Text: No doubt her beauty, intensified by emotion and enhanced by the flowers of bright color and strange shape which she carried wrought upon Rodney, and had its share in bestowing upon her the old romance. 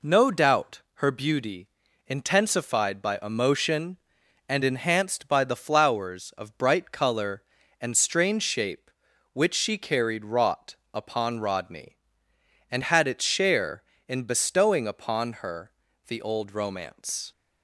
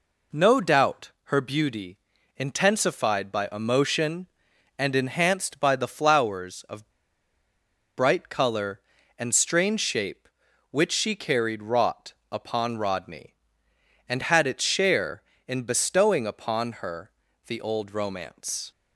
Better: first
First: pauses between "wrought" and "upon"; slight; at 10.7 s; 0.18 s long // pauses between "her" and "the"; slight; at 15.7 s; 0.36 s long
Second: pauses between "of" and "bright"; at 6.8 s; 1.0 s long // pauses between "wrought" and "upon"; slight; at 12.1 s; 0.18 s long // pauses between "her" and "the"; slight; at 17.1 s; 0.36 s long

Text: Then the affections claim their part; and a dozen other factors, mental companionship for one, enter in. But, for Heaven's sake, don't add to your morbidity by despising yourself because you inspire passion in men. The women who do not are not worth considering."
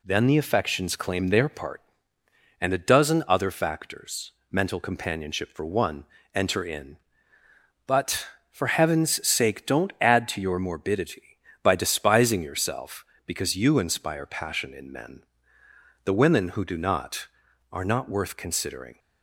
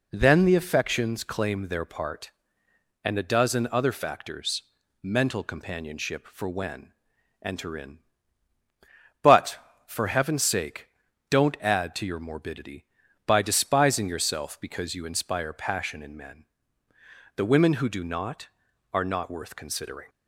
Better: first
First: none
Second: says "when" for "one"; at 6.4 s

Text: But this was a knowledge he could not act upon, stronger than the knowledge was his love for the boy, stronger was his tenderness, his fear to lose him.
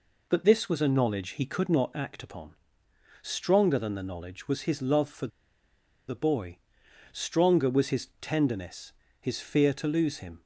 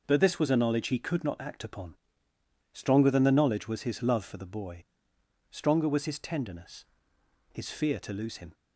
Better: second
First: pauses between "for" and "the"; noticeable; at 5.2 s; 0.80 s long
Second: none

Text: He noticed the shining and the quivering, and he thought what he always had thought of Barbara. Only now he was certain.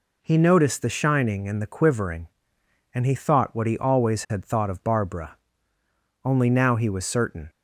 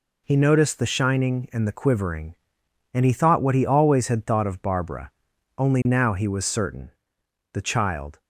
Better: first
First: none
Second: goes on to say "The child"; noticeable; from 7.5 s on; 0.66 s long

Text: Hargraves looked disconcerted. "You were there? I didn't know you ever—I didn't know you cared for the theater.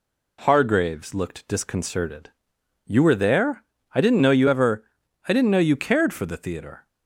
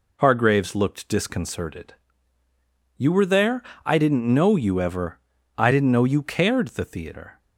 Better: first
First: none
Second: skips "for"; at 6.6 s

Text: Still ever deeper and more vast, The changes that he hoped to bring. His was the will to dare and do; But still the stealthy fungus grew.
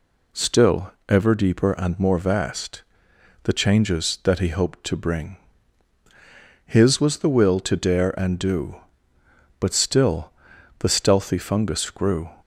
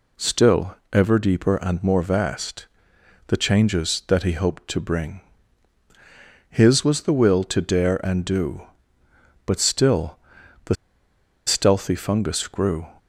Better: first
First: pauses between "Still" and "ever"; slight; at 0.9 s; 0.18 s long // pauses between "still" and "the"; noticeable; at 10.3 s; 0.50 s long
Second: pauses between "Still" and "ever"; slight; at 0.7 s; 0.18 s long // pauses between "still" and "the"; noticeable; at 10.1 s; 0.50 s long // pauses between "the" and "stealthy"; noticeable; at 10.7 s; 0.71 s long

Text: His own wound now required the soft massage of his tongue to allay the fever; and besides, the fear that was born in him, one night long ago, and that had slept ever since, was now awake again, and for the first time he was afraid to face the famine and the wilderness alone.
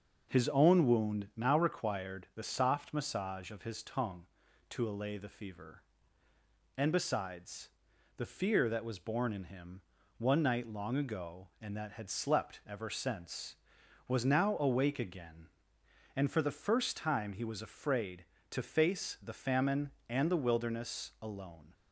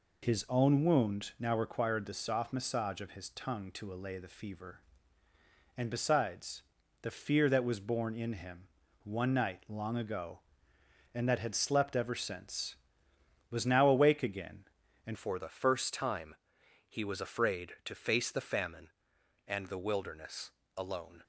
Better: first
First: none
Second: changes voice at "for"; from 15.1 s on; 6.1 s long // pauses between "time" and "he"; noticeable; at 16.3 s; 0.56 s long // pauses between "wilderness" and "alone"; slight; at 20.4 s; 0.26 s long

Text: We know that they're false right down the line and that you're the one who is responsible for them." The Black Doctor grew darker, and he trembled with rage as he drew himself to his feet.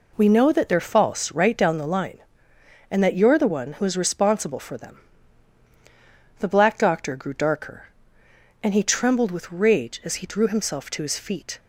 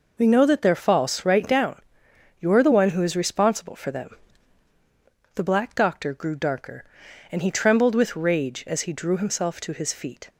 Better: first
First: none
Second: skips "the line and that"; at 2.0 s

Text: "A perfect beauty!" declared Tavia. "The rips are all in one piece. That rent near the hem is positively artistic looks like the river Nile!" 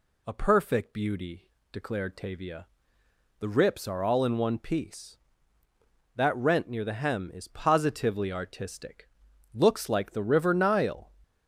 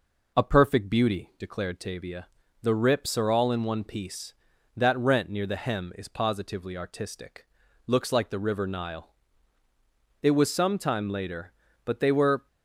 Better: first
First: pauses between "artistic" and "looks"; noticeable; at 9.0 s; 0.46 s long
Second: pauses between "artistic" and "looks"; at 7.4 s; 0.40 s long // goes on to say "It was some time later but they were"; strong; from 10.2 s on; 2.2 s long

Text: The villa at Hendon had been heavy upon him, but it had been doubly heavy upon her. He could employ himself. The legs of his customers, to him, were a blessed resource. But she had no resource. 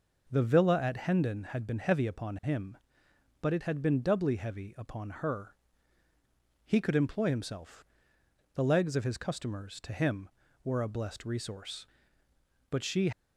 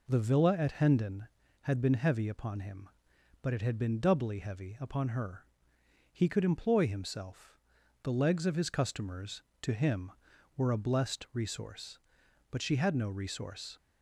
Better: second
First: stops before "had no resource"; at 13.1 s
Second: none

